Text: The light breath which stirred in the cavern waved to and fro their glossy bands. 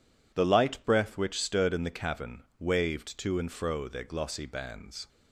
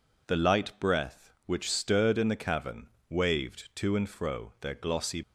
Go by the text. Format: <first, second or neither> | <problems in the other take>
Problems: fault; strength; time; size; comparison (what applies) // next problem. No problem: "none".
first | pauses between "cavern" and "waved"; slight; at 2.8 s; 0.20 s long // stops before "bands"; at 5.2 s